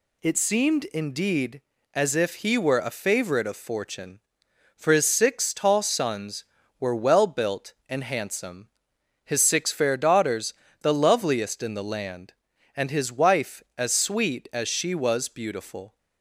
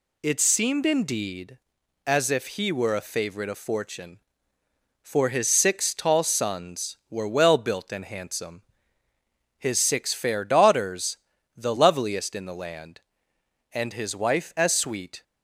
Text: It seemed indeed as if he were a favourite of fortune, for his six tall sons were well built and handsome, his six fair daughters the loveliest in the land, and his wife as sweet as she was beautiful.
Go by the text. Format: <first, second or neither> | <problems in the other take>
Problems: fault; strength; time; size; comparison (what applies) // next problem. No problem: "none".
first | pauses between "daughters" and "the"; at 11.1 s; 0.40 s long; slight in the first // stops before "as she was beautiful"; at 15.2 s